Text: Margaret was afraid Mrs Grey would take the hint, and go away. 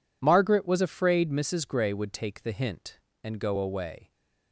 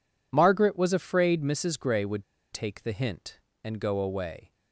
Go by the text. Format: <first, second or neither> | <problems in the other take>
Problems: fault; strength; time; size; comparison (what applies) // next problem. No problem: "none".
first | pauses between "would" and "take"; slight; at 2.2 s; 0.29 s long